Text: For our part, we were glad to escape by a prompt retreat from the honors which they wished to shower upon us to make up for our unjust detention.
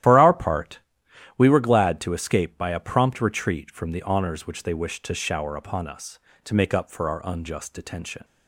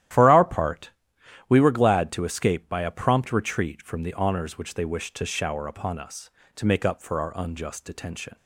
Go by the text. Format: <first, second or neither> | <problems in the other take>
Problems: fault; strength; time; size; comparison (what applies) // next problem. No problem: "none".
second | loses the start of "For"; at 0.0 s; 40 ms // starts louder than the rest; strong; until 1.6 s; 12.5 dB; strong in the second